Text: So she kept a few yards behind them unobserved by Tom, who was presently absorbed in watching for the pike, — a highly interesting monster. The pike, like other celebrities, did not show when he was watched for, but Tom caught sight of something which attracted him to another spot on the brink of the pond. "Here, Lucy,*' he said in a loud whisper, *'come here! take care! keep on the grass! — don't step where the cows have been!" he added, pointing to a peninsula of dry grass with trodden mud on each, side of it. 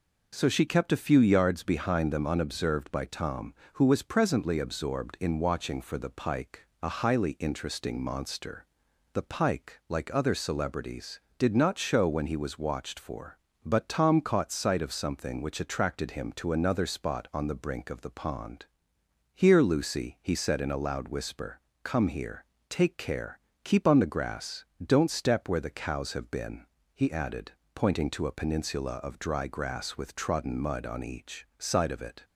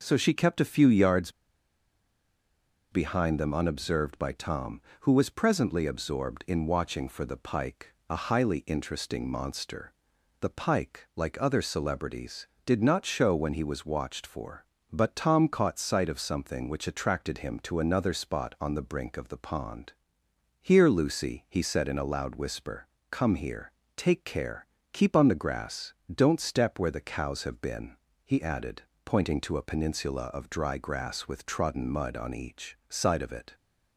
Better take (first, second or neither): first